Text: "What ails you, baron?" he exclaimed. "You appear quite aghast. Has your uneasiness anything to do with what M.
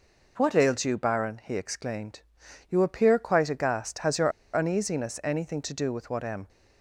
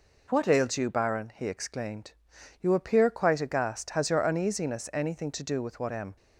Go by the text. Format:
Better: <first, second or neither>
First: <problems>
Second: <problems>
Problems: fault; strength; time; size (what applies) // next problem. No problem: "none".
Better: second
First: pauses between "your" and "uneasiness"; slight; at 4.3 s; 0.24 s long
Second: none